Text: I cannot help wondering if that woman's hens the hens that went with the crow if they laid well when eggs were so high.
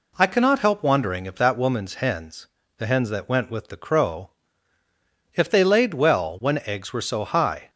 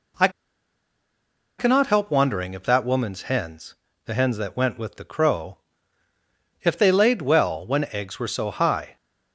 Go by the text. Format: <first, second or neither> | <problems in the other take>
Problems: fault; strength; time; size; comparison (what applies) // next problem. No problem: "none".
first | pauses between "I" and "cannot"; strong; at 0.2 s; 1.2 s long // pauses between "hens" and "the"; slight; at 3.7 s; 0.32 s long; slight in the first // pauses between "crow" and "if"; at 5.5 s; 1.0 s long; also in the first